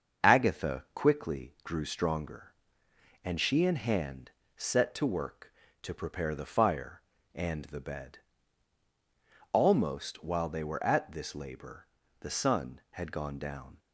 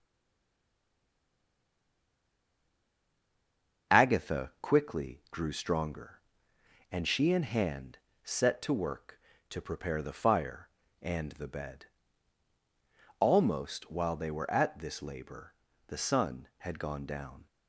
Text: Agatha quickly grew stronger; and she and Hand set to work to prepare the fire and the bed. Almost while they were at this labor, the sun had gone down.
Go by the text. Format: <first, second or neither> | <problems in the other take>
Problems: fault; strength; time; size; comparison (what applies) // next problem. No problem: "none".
first | stays silent before the first word; strong; until 3.8 s; 3.8 s long // starts louder than the rest; until 4.9 s; 6.5 dB; also in the first // pauses between "Hand" and "set"; slight; at 7.9 s; 0.24 s long; slight in the first